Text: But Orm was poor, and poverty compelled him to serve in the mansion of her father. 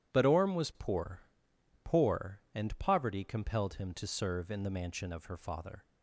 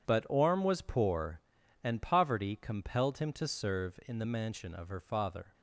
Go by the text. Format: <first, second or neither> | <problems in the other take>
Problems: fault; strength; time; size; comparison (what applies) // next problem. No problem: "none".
second | says "poor" twice; at 1.8 s